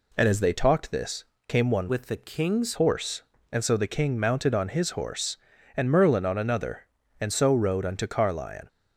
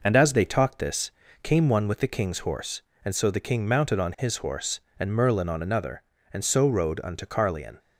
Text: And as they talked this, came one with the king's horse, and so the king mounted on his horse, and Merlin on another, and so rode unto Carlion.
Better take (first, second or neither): second